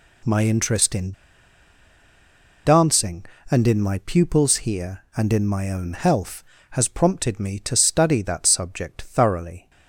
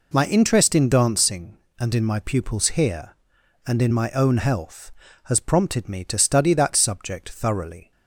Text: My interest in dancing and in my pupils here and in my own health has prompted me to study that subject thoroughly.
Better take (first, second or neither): second